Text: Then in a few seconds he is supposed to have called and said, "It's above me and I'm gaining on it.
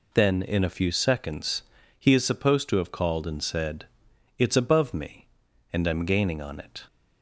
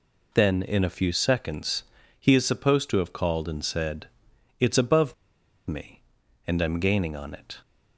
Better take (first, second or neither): first